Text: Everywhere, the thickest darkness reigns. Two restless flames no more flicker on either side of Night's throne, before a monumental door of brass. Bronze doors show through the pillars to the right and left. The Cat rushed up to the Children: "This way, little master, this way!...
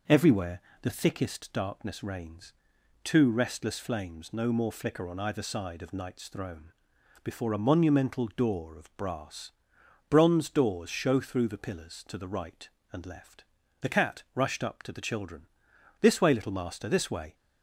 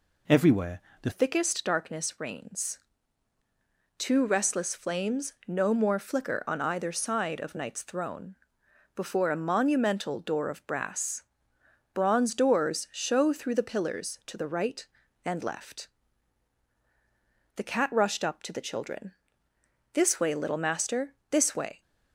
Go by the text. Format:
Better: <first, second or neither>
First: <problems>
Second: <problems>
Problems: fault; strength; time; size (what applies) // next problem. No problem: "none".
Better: first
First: none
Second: changes voice at "thickest"; from 1.1 s on; 20.7 s long